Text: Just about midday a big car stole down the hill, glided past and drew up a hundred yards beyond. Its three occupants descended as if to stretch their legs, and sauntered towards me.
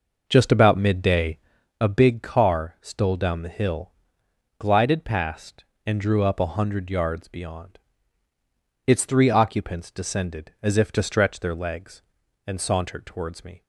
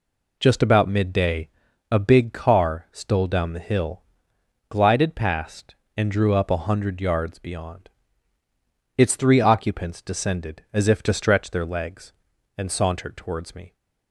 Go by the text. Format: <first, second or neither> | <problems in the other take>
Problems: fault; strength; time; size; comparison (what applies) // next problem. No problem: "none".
second | starts louder than the rest; noticeable; until 1.8 s; 5.5 dB // pauses between "midday" and "a"; at 1.3 s; 0.44 s long; also in the second